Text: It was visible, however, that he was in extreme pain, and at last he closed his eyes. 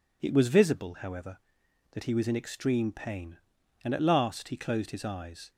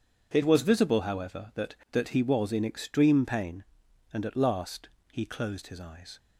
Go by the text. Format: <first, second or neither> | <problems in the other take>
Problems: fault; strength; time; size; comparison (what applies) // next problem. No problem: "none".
first | says "that" twice; at 1.8 s // pauses between "last" and "he"; slight; at 4.8 s; 0.22 s long